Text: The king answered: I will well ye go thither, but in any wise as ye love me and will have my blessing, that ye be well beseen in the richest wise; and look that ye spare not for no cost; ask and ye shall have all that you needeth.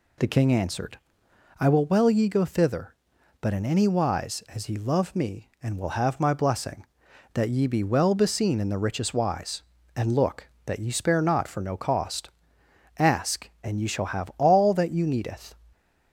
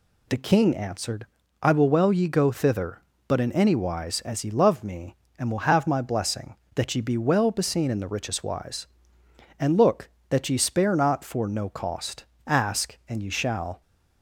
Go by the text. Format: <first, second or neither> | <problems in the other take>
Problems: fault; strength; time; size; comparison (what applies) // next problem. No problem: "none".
first | stops before "have all that you needeth"; at 13.8 s